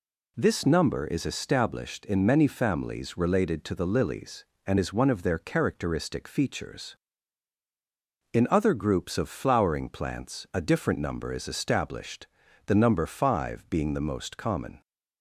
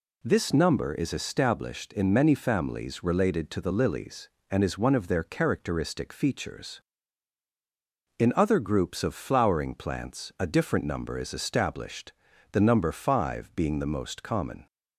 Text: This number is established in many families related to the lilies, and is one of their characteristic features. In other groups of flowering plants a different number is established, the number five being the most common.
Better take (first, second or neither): neither